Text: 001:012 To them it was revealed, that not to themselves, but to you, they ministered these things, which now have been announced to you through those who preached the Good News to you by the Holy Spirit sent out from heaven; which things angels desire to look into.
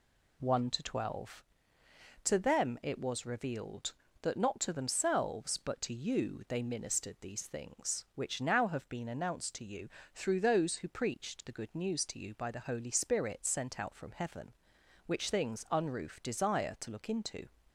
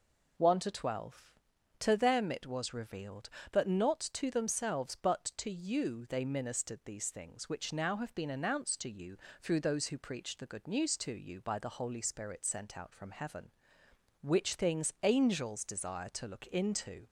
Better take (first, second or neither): second